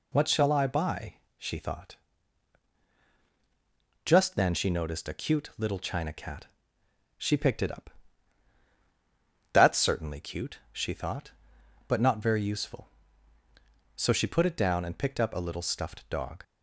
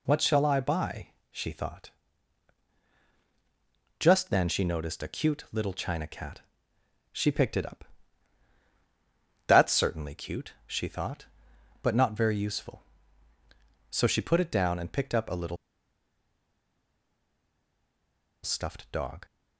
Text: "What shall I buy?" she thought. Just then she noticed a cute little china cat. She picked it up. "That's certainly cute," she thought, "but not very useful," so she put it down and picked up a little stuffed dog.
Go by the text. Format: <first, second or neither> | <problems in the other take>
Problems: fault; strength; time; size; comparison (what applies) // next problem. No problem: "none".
first | pauses between "little" and "stuffed"; strong; at 15.5 s; 2.8 s long